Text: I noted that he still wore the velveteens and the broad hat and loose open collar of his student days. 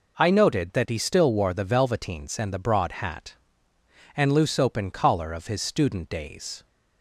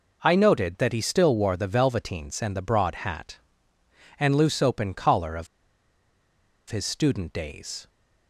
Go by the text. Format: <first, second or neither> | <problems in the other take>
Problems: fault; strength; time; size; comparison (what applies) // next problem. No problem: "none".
first | pauses between "of" and "his"; at 5.4 s; 1.2 s long